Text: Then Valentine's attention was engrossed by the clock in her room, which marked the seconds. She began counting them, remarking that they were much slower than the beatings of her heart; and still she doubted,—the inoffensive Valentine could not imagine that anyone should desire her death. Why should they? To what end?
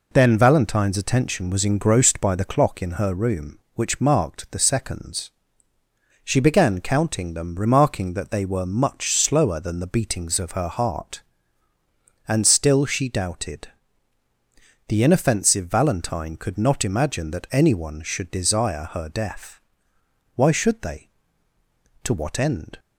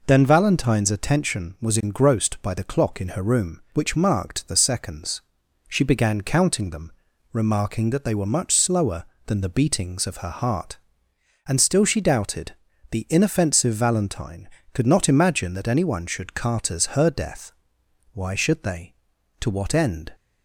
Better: first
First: none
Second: says "carters" for "desire"; at 16.3 s

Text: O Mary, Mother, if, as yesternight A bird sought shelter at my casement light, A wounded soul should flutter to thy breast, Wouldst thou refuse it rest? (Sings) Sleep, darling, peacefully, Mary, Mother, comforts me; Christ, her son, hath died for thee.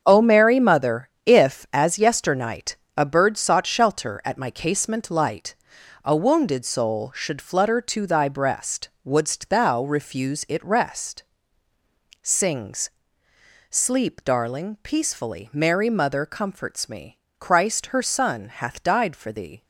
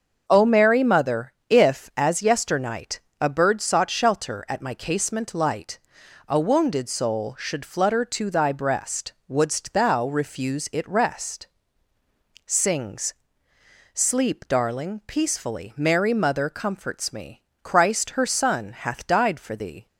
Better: second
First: gets quieter; strong; throughout; 9.5 dB // starts louder than the rest; until 1.0 s; 7 dB // pauses between "yesternight" and "A"; slight; at 2.7 s; 0.22 s long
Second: starts louder than the rest; until 1.2 s; 6.5 dB // pauses between "yesternight" and "A"; slight; at 2.9 s; 0.22 s long

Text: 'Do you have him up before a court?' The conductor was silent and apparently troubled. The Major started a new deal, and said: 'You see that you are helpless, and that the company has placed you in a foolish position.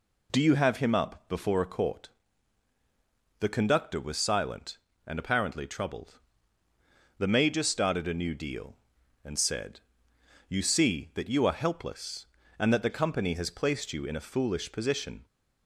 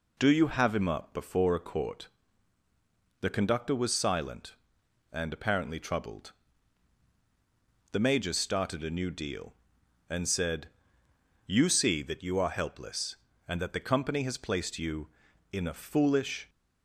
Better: first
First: none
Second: stops before "position"; at 16.4 s

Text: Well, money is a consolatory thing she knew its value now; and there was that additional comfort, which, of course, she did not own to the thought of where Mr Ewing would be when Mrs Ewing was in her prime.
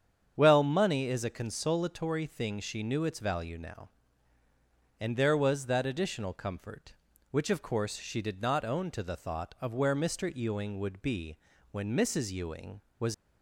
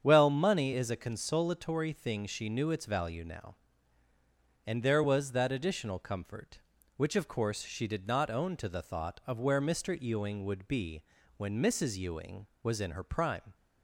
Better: second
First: starts louder than the rest; strong; until 1.3 s; 8 dB // pauses between "be" and "when"; at 11.3 s; 0.38 s long // stops before "in her prime"; at 13.1 s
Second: starts louder than the rest; strong; until 1.0 s; 7.5 dB // pauses between "be" and "when"; at 11.0 s; 0.38 s long

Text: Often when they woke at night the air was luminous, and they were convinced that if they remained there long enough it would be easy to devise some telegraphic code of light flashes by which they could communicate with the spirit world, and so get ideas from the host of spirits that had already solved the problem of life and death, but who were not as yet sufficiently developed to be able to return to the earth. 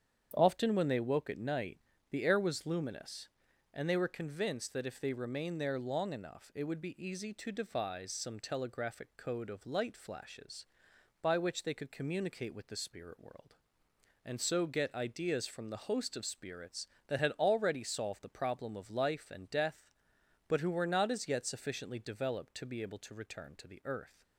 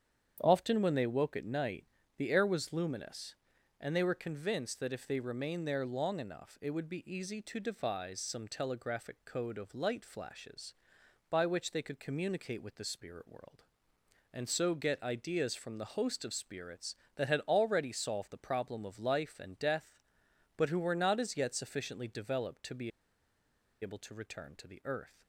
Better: first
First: starts louder than the rest; strong; until 1.3 s; 8.5 dB // pauses between "night" and "the"; slight; at 1.7 s; 0.32 s long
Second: starts louder than the rest; strong; until 1.4 s; 8.5 dB // pauses between "night" and "the"; slight; at 1.8 s; 0.32 s long // pauses between "be" and "able"; noticeable; at 22.9 s; 0.91 s long

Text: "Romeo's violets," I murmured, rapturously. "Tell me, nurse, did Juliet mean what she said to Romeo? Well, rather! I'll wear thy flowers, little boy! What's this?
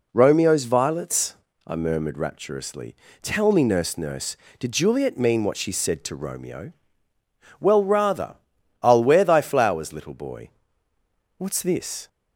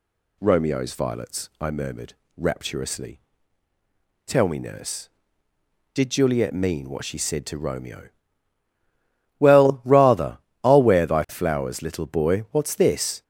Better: second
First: says "nurse" twice; at 3.9 s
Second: none

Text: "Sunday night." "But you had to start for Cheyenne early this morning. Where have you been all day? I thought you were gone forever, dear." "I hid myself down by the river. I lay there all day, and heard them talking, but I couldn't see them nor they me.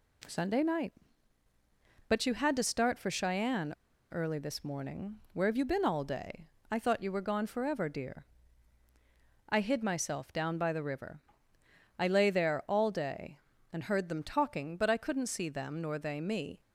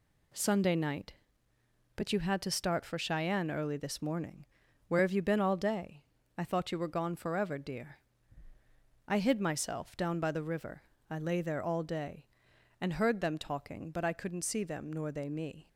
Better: second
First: pauses between "Cheyenne" and "early"; at 3.7 s; 0.37 s long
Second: none

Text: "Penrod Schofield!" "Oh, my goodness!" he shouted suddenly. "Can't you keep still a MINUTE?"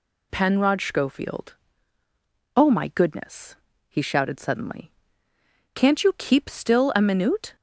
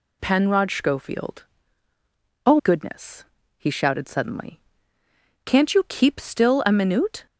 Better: first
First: none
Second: skips "my"; at 2.5 s

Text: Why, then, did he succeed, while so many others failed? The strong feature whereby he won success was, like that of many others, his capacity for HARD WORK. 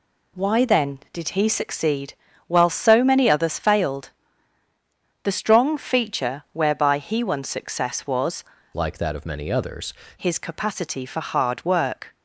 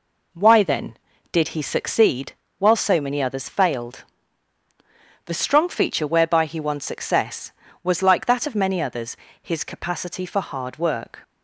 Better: second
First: changes voice from "like" to "others"; from 8.7 to 9.9 s; 1.2 s long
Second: none

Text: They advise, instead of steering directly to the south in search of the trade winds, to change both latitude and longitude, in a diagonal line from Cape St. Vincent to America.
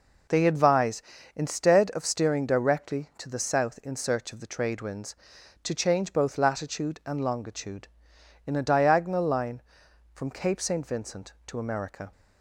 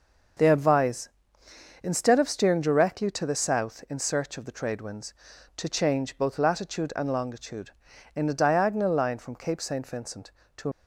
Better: first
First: none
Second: starts louder than the rest; noticeable; until 2.1 s; 6 dB // stops before "America"; at 10.7 s

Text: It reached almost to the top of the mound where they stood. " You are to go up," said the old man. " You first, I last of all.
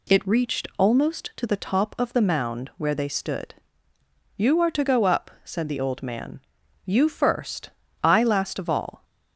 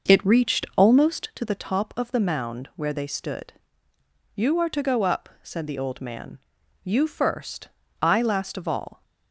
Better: first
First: none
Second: starts louder than the rest; until 1.5 s; 6.5 dB

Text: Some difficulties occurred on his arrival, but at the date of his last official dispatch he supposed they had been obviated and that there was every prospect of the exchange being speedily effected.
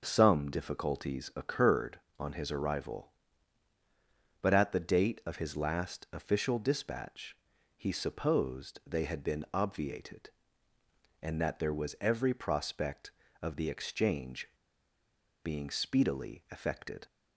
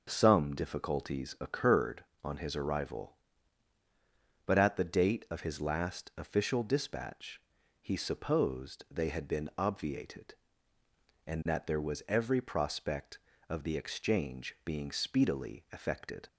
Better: second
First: pauses between "dispatch" and "he"; at 7.3 s; 0.40 s long // pauses between "exchange" and "being"; noticeable; at 14.4 s; 0.98 s long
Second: pauses between "dispatch" and "he"; at 7.4 s; 0.40 s long

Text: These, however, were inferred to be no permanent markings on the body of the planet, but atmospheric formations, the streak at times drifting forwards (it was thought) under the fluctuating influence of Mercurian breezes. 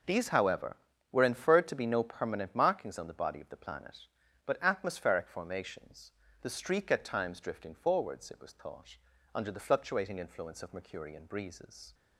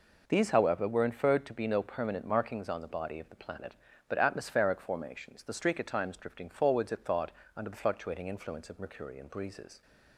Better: first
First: none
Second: skips "was"; at 7.0 s

